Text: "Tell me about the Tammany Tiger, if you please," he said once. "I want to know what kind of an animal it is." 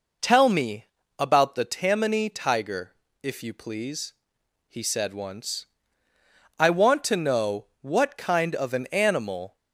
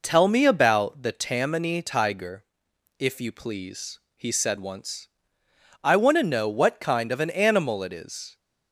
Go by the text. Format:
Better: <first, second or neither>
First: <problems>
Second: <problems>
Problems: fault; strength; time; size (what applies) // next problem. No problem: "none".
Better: second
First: pauses between "me" and "about"; slight; at 0.8 s; 0.34 s long // stops before "it is"; at 9.5 s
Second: none